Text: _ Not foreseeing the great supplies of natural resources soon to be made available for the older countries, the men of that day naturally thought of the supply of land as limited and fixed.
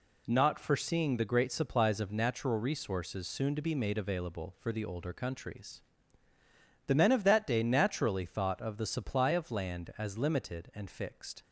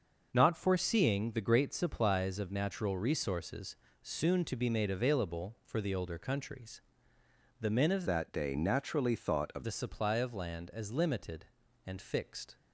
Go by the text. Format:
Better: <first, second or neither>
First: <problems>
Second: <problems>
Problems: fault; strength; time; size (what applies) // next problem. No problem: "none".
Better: first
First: none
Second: starts louder than the rest; noticeable; until 1.3 s; 6 dB // pauses between "resources" and "soon"; slight; at 3.7 s; 0.26 s long // changes voice from "that" to "of"; from 8.0 to 9.6 s; 1.6 s long